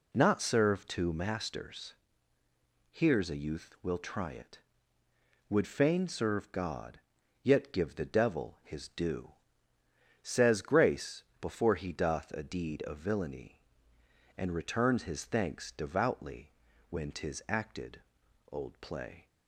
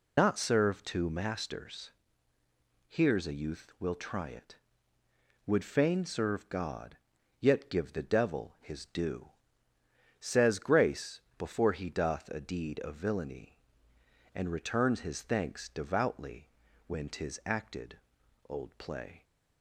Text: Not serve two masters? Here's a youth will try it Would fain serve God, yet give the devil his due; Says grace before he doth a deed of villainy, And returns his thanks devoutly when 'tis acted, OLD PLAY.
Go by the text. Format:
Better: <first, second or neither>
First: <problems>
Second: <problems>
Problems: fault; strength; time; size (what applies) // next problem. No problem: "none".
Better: first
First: pauses between "grace" and "before"; slight; at 11.2 s; 0.18 s long // pauses between "devoutly" and "when"; slight; at 16.5 s; 0.36 s long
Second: loses the start of "Not"; at 0.1 s; 65 ms // pauses between "grace" and "before"; slight; at 11.2 s; 0.18 s long // pauses between "devoutly" and "when"; slight; at 16.4 s; 0.36 s long